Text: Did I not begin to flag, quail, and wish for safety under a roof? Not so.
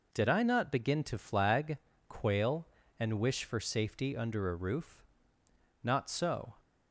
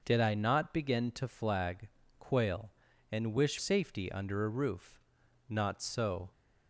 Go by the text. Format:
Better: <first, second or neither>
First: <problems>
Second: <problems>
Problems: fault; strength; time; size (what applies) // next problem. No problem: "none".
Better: first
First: none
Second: starts louder than the rest; noticeable; until 1.0 s; 6 dB // skips "for"; at 3.5 s